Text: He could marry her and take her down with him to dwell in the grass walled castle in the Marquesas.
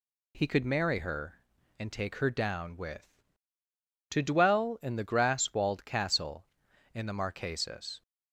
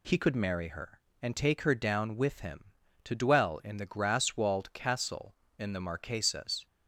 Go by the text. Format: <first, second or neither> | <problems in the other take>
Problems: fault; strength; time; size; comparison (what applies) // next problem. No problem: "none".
second | skips "him"; at 3.6 s